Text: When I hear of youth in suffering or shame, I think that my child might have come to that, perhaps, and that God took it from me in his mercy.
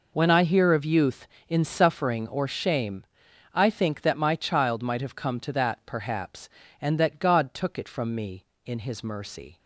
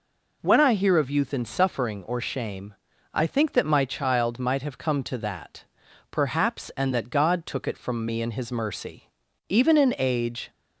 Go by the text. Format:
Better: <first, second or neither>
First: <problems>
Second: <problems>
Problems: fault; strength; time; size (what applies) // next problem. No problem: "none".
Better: first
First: none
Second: goes on to say "Even in age"; noticeable; from 9.4 s on; 1.0 s long